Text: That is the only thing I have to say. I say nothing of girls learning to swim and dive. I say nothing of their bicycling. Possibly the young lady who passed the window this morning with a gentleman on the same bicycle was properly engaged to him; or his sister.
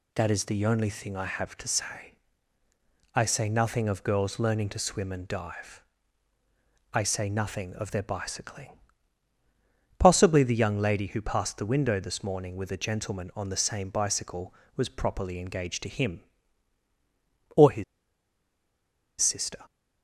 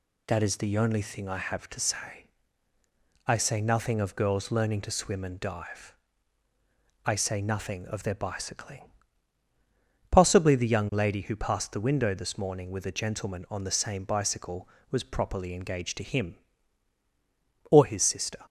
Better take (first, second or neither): second